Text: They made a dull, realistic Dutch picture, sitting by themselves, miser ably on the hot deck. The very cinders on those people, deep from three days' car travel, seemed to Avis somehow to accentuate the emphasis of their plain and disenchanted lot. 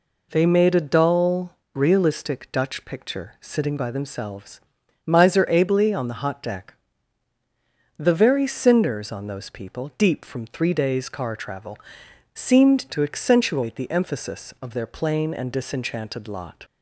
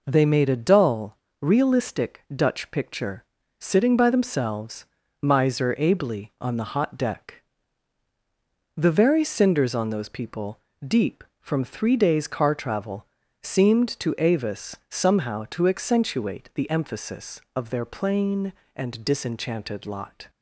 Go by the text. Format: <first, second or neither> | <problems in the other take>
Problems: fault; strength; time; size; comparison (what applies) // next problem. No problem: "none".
second | skips "to Avis somehow"; at 12.8 s